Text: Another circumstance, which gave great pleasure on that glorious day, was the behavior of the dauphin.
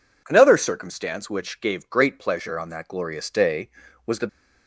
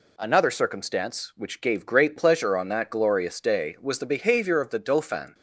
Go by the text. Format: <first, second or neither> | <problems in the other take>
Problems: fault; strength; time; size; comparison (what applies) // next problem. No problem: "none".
second | stops before "behavior of the dauphin"; at 4.2 s